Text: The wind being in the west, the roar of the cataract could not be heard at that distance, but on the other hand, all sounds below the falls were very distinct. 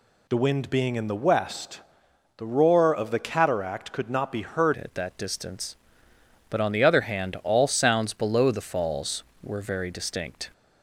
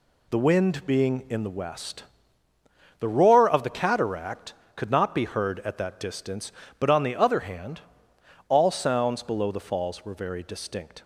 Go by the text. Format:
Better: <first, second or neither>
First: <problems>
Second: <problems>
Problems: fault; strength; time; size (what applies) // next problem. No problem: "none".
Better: second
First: changes voice at "at"; from 4.8 s on; 5.7 s long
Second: none